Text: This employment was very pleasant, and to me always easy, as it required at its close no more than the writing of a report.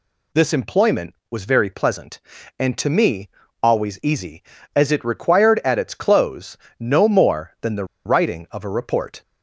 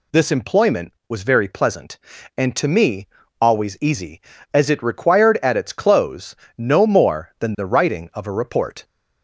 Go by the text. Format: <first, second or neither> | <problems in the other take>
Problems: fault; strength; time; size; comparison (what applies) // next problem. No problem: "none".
second | pauses between "me" and "always"; slight; at 3.2 s; 0.34 s long; slight in the second // pauses between "close" and "no"; slight; at 6.5 s; 0.24 s long; slight in the second // pauses between "the" and "writing"; slight; at 7.8 s; 0.21 s long